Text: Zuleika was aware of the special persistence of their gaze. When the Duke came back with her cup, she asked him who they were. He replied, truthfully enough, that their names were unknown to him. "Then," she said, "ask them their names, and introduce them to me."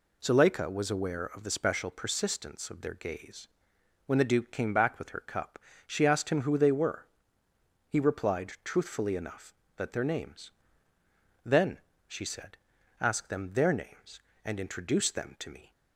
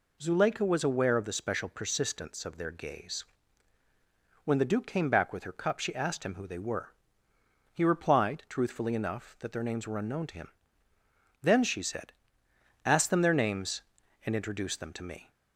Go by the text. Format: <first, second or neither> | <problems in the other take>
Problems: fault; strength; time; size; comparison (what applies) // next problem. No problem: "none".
second | skips "were unknown to him"; at 10.9 s